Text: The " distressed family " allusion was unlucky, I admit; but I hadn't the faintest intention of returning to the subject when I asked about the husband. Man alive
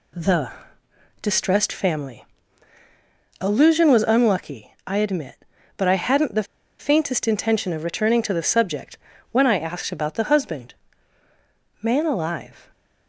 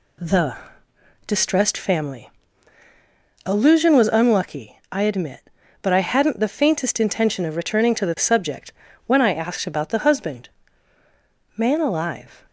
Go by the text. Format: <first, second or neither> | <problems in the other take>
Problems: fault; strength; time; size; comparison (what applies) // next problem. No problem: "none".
second | pauses between "the" and "faintest"; slight; at 6.4 s; 0.33 s long // pauses between "subject" and "when"; slight; at 8.9 s; 0.36 s long; slight in the second